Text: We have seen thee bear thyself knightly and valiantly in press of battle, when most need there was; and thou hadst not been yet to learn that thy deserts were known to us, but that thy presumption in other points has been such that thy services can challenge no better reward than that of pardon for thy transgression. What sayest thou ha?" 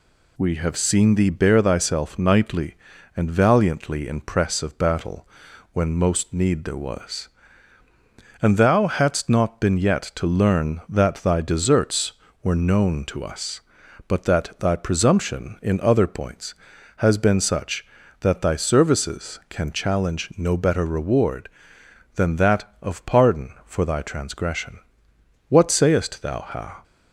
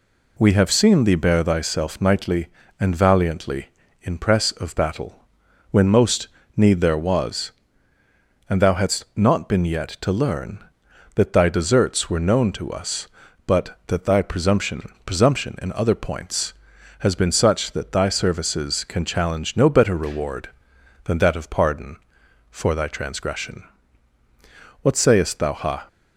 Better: first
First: none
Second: pauses between "most" and "need"; slight; at 6.2 s; 0.28 s long // says "presumption" twice; at 15.0 s

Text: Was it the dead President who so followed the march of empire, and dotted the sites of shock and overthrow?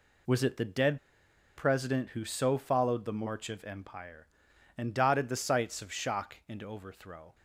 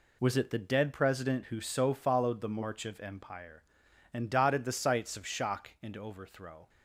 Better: second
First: pauses between "dead" and "President"; noticeable; at 0.9 s; 0.57 s long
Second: none

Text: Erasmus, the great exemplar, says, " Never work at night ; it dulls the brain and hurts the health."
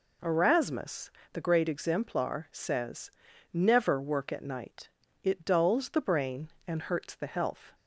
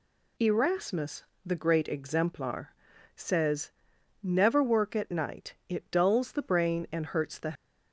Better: first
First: none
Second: stops before "health"; at 7.5 s

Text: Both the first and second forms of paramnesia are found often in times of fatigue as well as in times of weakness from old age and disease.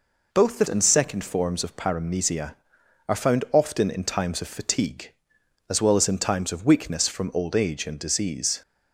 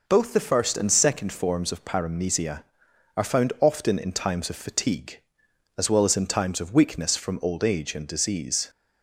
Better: second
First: skips "first"; at 0.6 s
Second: none

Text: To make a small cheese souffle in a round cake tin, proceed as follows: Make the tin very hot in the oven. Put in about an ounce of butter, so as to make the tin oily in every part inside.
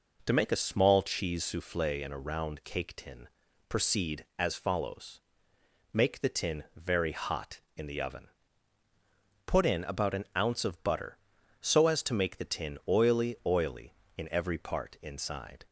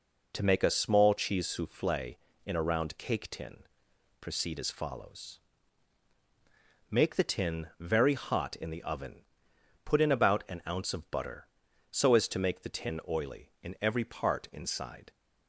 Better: second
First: says "oily" twice; at 13.4 s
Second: none

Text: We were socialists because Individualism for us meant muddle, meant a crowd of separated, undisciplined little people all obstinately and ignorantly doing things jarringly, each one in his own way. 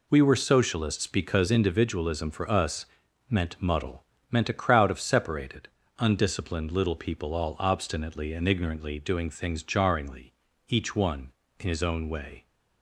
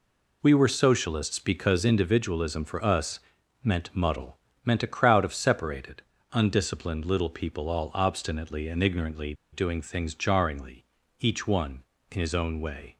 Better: first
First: pauses between "us" and "meant"; at 2.8 s; 0.44 s long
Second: pauses between "us" and "meant"; at 3.1 s; 0.44 s long // pauses between "ignorantly" and "doing"; slight; at 9.3 s; 0.18 s long

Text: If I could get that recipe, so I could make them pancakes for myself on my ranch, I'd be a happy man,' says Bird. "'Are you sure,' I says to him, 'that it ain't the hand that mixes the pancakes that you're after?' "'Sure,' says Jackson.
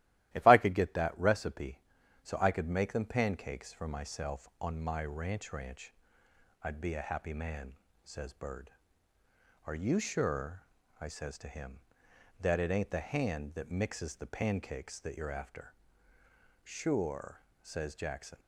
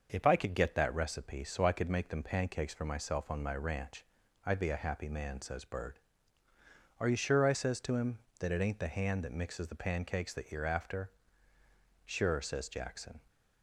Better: second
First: starts louder than the rest; strong; until 1.3 s; 14.5 dB // says "ranch" twice; at 5.5 s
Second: starts louder than the rest; noticeable; until 1.1 s; 6 dB

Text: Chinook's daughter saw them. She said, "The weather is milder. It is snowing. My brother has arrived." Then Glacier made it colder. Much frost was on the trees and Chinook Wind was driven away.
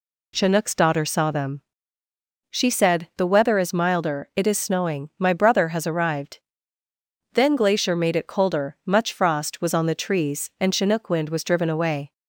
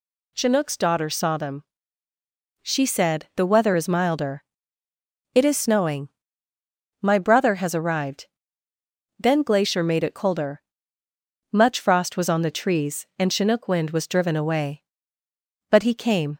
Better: first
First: none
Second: goes on to say "But he came"; noticeable; from 15.6 s on; 0.68 s long

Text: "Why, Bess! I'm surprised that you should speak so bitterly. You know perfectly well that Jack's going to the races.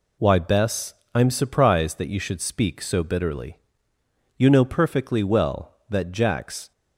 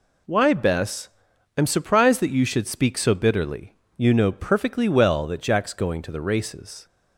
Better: second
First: stops before "going to the races"; at 6.7 s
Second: none

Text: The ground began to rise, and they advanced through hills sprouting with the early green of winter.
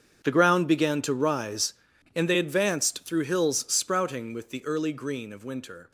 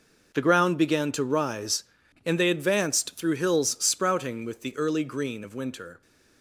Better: second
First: gets quieter; strong; throughout; 16 dB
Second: none

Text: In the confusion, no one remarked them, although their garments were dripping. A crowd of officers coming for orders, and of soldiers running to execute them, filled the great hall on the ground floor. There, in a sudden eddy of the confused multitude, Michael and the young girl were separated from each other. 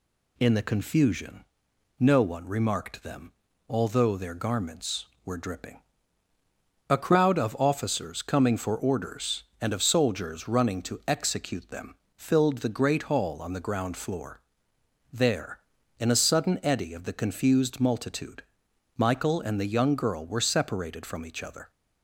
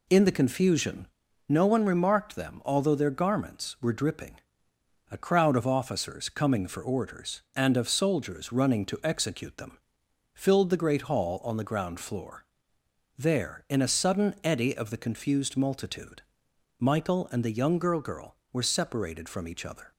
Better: first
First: none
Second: says "girl" twice; at 17.9 s

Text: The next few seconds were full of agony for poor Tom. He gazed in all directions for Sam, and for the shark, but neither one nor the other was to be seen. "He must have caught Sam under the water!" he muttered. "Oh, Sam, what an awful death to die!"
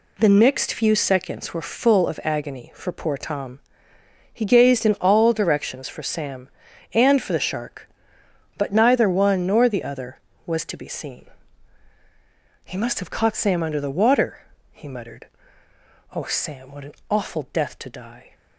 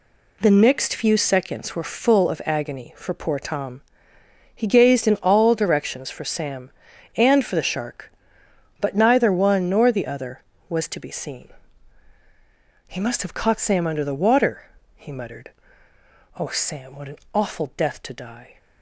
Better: neither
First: pauses between "an" and "awful"; slight; at 16.9 s; 0.16 s long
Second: pauses between "an" and "awful"; slight; at 17.1 s; 0.16 s long

